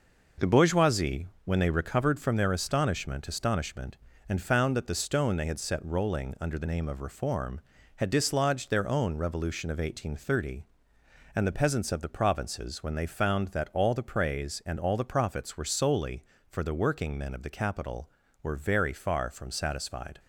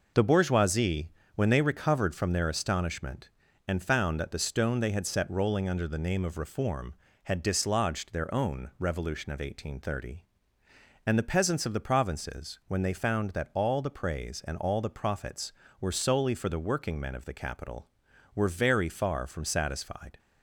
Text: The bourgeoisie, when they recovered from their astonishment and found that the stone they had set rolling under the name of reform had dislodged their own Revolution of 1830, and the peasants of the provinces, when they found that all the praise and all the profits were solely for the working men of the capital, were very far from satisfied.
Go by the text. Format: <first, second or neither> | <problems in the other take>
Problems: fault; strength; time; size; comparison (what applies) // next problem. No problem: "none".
second | says "astonishment" twice; at 3.2 s